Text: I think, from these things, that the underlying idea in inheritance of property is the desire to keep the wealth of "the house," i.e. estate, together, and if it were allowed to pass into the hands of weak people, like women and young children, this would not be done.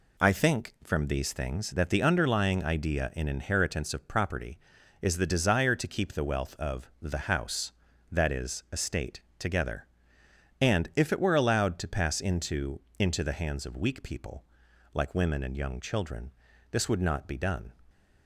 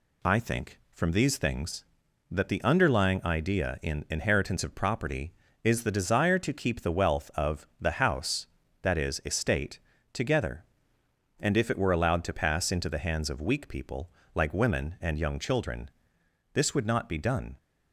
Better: second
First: says "into" twice; at 12.9 s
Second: none

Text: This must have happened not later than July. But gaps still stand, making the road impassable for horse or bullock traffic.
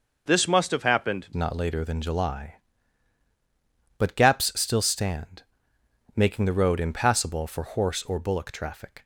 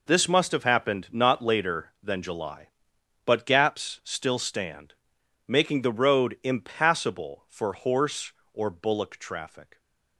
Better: second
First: changes voice at "not"; from 1.3 s on; 7.7 s long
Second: none

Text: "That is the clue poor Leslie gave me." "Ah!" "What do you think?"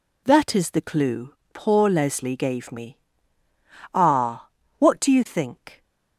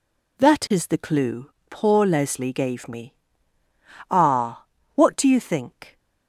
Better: neither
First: pauses between "clue" and "poor"; slight; at 1.3 s; 0.18 s long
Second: pauses between "clue" and "poor"; slight; at 1.4 s; 0.18 s long

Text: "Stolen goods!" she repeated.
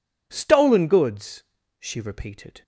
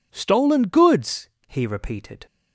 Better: first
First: none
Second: says "he" for "she"; at 1.4 s

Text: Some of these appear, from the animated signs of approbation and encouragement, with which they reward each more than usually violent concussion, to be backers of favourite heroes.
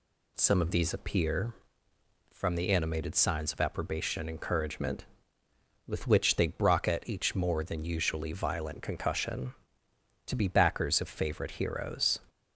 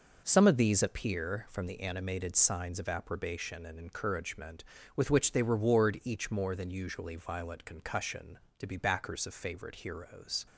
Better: second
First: says "brocket" for "reward"; at 6.4 s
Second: none

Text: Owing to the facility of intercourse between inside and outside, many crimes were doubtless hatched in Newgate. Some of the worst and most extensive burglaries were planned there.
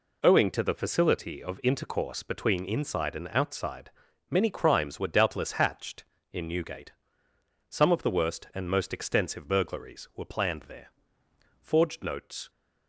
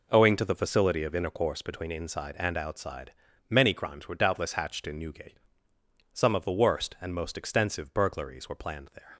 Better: second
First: goes on to say "Forged notes"; noticeable; from 11.6 s on; 0.88 s long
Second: none

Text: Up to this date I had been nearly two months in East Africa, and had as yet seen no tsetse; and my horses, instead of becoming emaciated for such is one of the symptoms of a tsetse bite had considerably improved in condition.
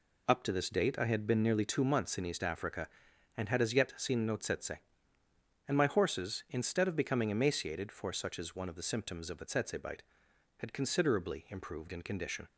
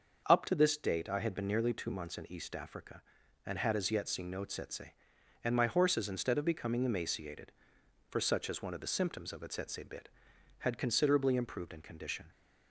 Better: first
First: none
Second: starts louder than the rest; until 1.2 s; 6.5 dB // says "bit" for "bite"; at 9.8 s

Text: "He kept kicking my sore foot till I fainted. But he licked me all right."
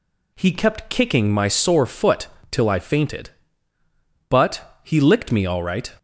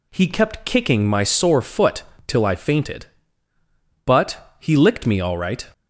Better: neither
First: pauses between "foot" and "till"; slight; at 2.2 s; 0.23 s long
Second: pauses between "foot" and "till"; slight; at 2.0 s; 0.24 s long

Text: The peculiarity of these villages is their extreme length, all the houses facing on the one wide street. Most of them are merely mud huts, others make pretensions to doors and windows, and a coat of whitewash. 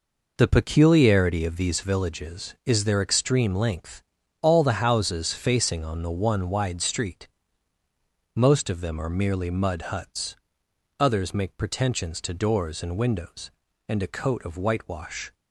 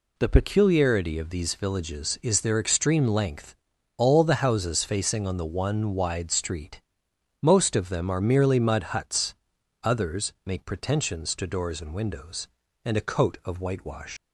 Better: first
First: none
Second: leaves "whitewash" unfinished; at 14.1 s; 135 ms

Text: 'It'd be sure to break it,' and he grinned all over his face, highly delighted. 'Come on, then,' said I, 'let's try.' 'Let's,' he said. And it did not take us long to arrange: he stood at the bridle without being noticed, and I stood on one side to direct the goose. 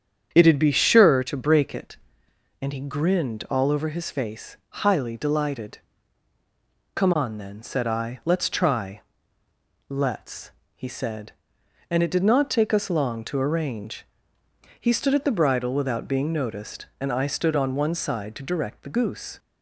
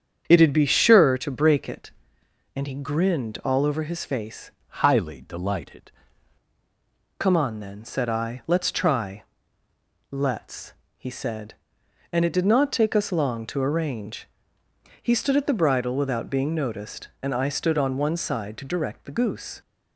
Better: first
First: starts louder than the rest; strong; until 1.3 s; 8 dB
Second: starts louder than the rest; strong; until 1.2 s; 8 dB // changes voice from "highly" to "delighted"; from 4.6 to 5.9 s; 1.3 s long

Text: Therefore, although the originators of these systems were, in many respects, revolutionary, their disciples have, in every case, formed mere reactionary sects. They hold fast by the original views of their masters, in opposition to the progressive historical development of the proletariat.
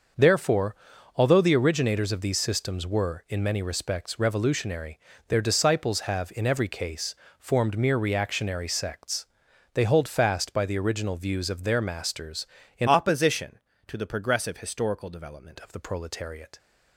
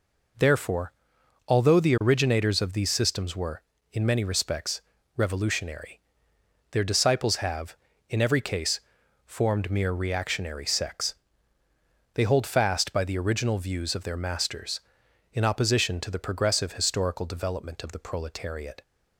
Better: second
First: starts louder than the rest; until 1.5 s; 6.5 dB // changes voice from "opposition" to "development"; from 12.8 to 15.5 s; 2.7 s long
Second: none

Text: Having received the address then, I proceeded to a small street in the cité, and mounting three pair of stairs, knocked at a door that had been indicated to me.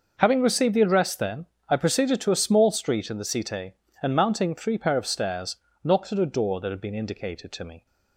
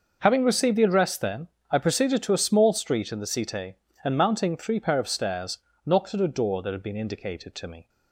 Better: neither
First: none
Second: none

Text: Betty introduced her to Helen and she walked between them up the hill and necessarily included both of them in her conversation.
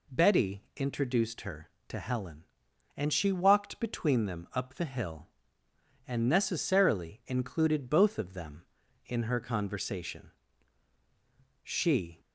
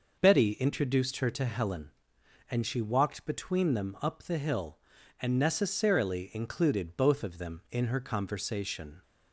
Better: second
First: goes on to say "She"; from 11.6 s on; 0.58 s long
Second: none

